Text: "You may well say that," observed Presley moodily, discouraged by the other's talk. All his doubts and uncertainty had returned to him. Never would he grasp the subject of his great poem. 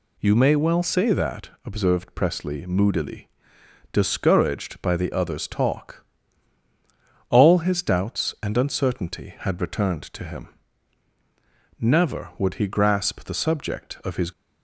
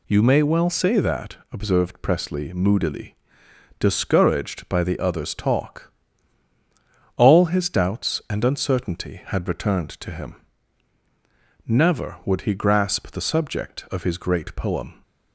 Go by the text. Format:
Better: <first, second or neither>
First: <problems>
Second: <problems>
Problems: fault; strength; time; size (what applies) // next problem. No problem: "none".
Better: second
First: stops before "great poem"; at 14.3 s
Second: none